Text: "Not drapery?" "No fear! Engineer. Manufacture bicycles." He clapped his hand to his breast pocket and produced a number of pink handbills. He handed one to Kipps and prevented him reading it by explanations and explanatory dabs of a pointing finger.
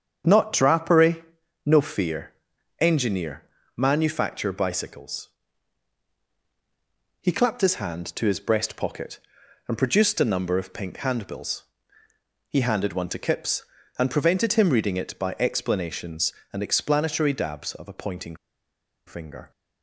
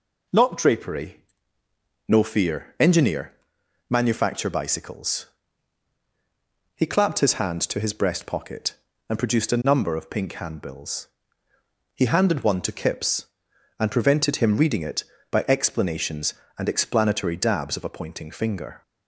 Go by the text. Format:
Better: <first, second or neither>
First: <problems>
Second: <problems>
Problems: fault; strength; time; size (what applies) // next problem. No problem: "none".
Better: second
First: starts louder than the rest; strong; until 1.7 s; 7.5 dB // pauses between "pointing" and "finger"; noticeable; at 18.3 s; 0.71 s long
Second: none